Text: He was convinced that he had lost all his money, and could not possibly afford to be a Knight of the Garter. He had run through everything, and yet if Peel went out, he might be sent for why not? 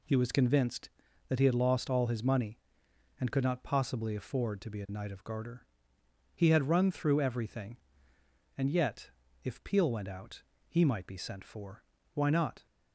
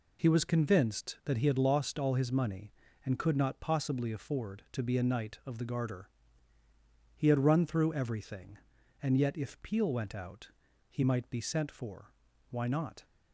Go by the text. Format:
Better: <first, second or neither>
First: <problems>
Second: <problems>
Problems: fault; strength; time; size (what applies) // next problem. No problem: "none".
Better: second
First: skips "the"; at 5.2 s // pauses between "yet" and "if"; slight; at 9.0 s; 0.34 s long // pauses between "for" and "why"; slight; at 11.8 s; 0.30 s long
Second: pauses between "for" and "why"; at 12.1 s; 0.40 s long